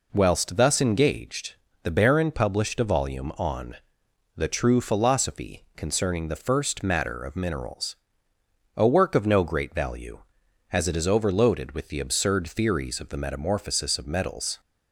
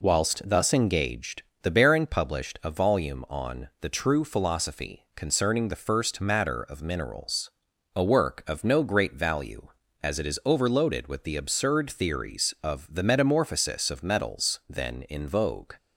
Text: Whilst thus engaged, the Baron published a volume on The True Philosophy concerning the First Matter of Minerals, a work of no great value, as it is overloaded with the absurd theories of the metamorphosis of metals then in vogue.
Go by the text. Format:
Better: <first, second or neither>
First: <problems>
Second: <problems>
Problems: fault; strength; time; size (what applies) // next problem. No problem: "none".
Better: second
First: pauses between "on" and "The"; noticeable; at 3.7 s; 0.60 s long // stops before "then in vogue"; at 14.5 s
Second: none